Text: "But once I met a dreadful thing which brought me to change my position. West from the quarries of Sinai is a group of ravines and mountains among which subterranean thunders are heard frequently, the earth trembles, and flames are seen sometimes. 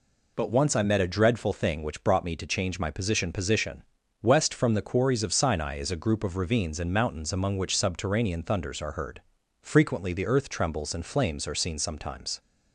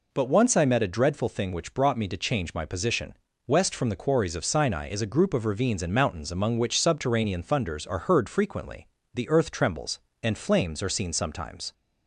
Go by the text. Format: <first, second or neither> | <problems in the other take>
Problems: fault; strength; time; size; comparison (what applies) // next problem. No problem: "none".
second | says "position" twice; at 3.3 s // pauses between "heard" and "frequently"; at 9.2 s; 0.42 s long